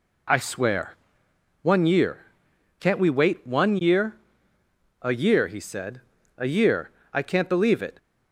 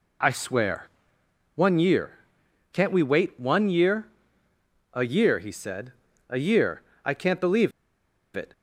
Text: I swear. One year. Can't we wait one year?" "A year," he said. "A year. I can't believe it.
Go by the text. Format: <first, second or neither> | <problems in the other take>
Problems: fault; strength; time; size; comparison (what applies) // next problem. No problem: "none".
first | pauses between "believe" and "it"; noticeable; at 7.7 s; 0.65 s long